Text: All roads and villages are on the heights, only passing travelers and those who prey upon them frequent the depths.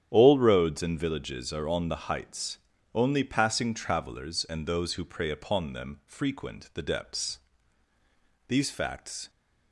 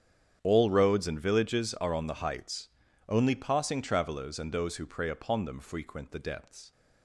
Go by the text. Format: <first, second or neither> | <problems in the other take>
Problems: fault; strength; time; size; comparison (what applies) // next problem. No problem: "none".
second | starts louder than the rest; strong; until 1.1 s; 9.5 dB; strong in the second // goes on to say "These facts"; noticeable; from 8.4 s on; 0.82 s long